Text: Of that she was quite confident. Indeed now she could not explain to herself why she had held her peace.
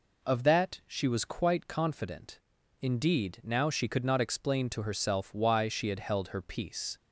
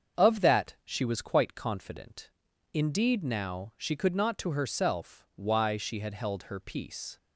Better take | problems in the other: first | starts louder than the rest; until 1.2 s; 7 dB // skips "explain"; at 4.3 s

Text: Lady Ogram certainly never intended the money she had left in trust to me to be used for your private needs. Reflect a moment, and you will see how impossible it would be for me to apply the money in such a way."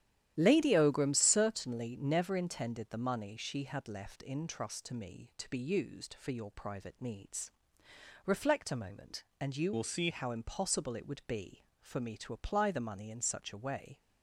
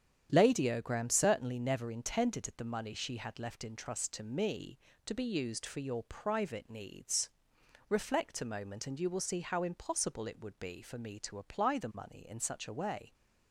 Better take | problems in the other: second | starts louder than the rest; strong; until 1.3 s; 11.5 dB; strong in the second // changes voice from "will" to "see"; from 9.7 to 10.0 s; 0.3 s long

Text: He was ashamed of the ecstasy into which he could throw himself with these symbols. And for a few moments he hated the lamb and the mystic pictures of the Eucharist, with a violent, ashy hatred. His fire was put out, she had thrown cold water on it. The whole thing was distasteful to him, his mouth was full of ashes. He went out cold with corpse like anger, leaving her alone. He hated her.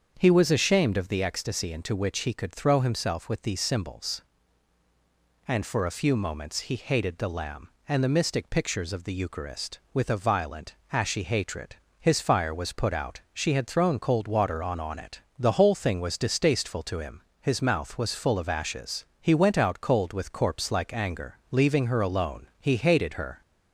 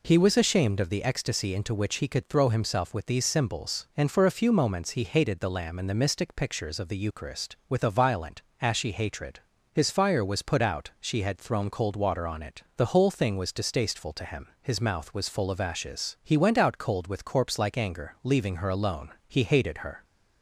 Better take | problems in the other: second | starts louder than the rest; until 1.1 s; 7 dB // says "on" twice; at 14.7 s

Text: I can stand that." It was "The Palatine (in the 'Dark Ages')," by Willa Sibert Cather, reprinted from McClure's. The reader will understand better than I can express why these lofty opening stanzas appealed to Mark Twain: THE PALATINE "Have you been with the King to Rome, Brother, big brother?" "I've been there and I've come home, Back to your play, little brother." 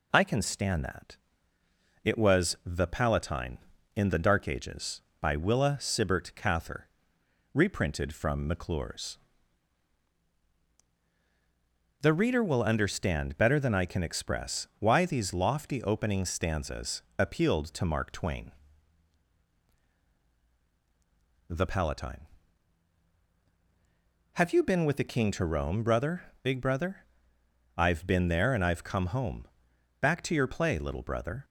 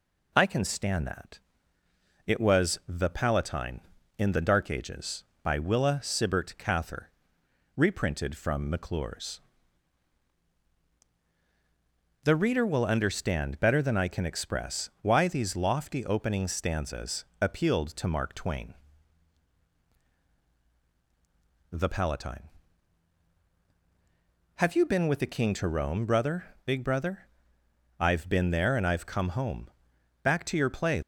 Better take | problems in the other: first | stops before "little brother"; at 31.0 s

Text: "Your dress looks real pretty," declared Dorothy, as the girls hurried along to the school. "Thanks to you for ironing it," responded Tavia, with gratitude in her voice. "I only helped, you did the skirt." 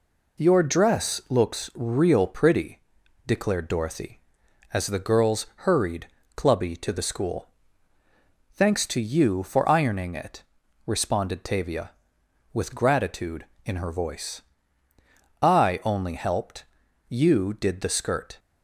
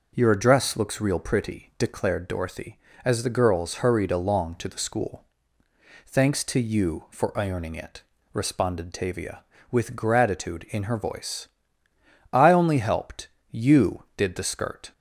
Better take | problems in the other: second | pauses between "girls" and "hurried"; slight; at 5.4 s; 0.20 s long // says "clubby" for "along"; at 6.3 s

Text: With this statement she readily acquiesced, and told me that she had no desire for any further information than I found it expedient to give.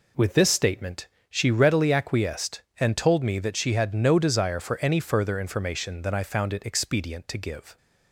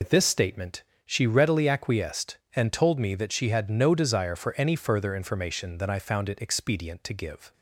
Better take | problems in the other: first | loses the start of "With"; at 0.0 s; 85 ms // pauses between "statement" and "she"; slight; at 0.8 s; 0.20 s long; slight in the first

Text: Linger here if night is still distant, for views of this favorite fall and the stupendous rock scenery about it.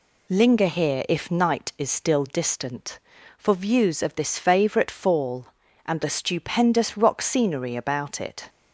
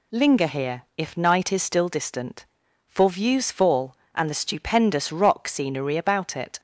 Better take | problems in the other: first | skips "of this favorite"; at 3.4 s

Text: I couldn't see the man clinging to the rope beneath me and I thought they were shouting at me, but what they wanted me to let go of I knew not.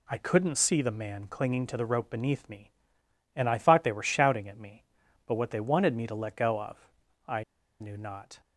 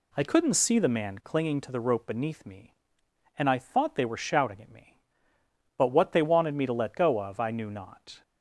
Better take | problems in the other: second | pauses between "of" and "I"; noticeable; at 6.7 s; 0.50 s long // pauses between "I" and "knew"; at 7.4 s; 0.36 s long

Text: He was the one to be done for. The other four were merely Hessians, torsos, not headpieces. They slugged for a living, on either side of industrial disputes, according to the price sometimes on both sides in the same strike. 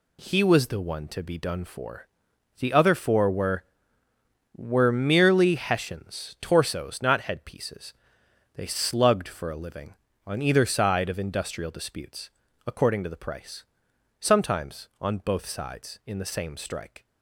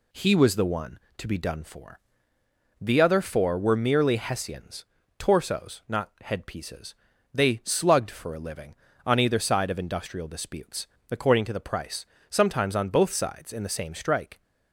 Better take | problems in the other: second | says "were" twice; at 4.5 s // pauses between "price" and "sometimes"; noticeable; at 13.6 s; 0.58 s long; slight in the second

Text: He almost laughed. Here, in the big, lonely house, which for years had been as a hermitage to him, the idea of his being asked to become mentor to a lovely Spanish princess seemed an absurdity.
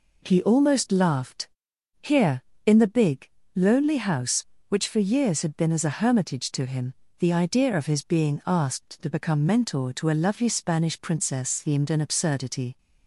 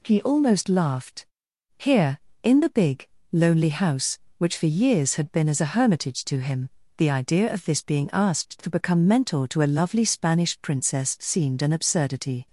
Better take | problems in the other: first | says "this" for "his"; at 7.6 s

